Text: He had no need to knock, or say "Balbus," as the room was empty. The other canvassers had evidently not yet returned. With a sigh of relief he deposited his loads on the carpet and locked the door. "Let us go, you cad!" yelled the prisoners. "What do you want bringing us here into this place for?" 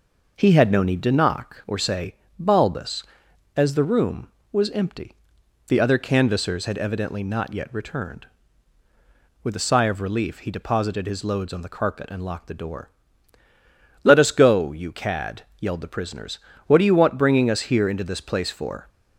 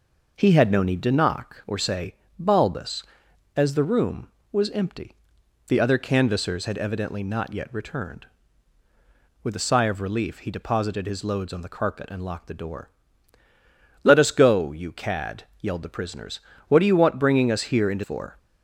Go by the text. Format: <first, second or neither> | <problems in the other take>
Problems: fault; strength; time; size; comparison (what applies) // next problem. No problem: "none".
first | pauses between "say" and "Balbus"; slight; at 2.1 s; 0.24 s long; slight in the first // skips "this place"; at 18.0 s